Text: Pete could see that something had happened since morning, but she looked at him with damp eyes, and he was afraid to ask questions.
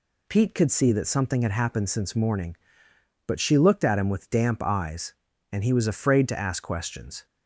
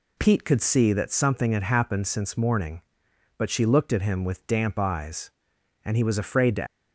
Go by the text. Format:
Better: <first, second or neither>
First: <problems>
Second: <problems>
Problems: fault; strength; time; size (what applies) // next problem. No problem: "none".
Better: first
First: none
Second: stops before "ask questions"; at 6.6 s